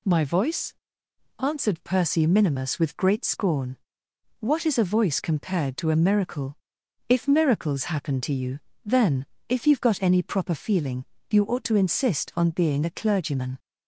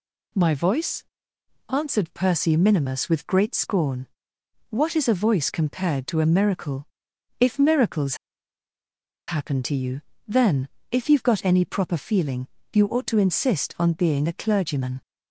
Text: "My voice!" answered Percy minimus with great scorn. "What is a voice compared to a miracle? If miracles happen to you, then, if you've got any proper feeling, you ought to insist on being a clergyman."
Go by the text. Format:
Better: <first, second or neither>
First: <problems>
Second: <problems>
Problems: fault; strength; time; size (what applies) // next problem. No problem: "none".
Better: first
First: none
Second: pauses between "miracles" and "happen"; at 8.1 s; 1.1 s long